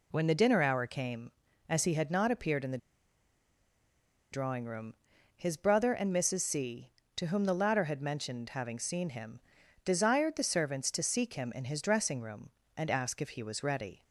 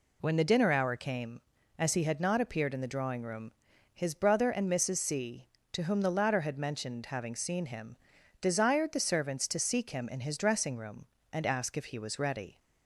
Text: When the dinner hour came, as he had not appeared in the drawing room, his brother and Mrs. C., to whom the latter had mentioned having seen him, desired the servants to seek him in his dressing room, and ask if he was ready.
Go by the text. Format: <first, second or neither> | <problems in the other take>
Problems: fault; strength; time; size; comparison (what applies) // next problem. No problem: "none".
second | pauses between "the" and "drawing"; strong; at 2.7 s; 1.5 s long